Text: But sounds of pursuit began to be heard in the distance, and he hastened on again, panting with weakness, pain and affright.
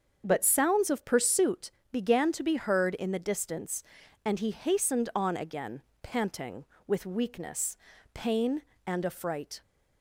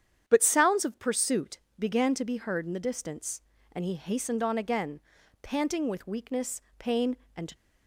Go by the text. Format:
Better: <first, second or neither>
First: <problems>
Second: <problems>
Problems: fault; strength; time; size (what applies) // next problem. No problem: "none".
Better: first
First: starts louder than the rest; until 1.2 s; 7 dB // pauses between "pursuit" and "began"; slight; at 1.6 s; 0.24 s long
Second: starts louder than the rest; strong; until 1.2 s; 9 dB // pauses between "pursuit" and "began"; slight; at 1.5 s; 0.20 s long // stops before "affright"; at 7.5 s